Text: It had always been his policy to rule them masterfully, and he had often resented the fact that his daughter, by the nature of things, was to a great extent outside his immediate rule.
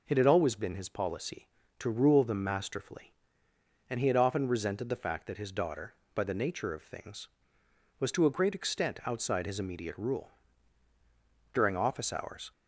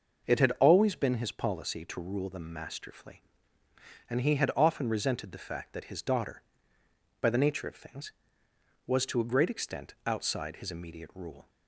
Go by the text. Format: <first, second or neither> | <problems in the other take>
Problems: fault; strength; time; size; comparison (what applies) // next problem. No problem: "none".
second | goes on to say "During office hours"; noticeable; from 11.5 s on; 0.98 s long